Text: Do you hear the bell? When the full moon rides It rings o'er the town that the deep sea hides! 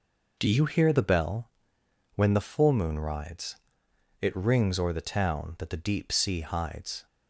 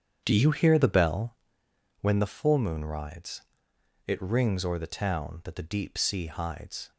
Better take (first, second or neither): first